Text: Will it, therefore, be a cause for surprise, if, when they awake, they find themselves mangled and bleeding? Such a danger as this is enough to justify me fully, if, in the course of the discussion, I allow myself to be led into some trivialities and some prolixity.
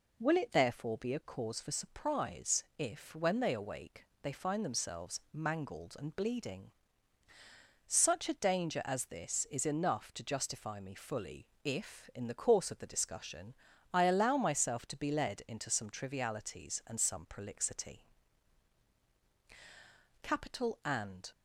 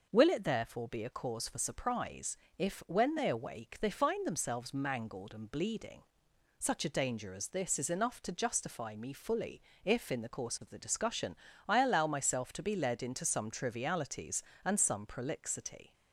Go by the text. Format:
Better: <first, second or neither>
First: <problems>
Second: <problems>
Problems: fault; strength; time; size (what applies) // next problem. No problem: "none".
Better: second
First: goes on to say "CAPITAL AND"; noticeable; from 20.2 s on; 1.1 s long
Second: none